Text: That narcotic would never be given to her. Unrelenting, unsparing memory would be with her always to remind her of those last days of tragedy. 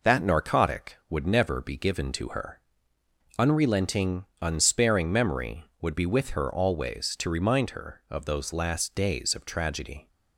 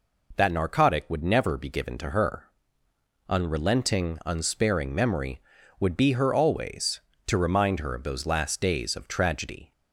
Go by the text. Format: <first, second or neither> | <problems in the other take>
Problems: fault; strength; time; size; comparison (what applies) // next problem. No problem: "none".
first | skips "with"; at 6.1 s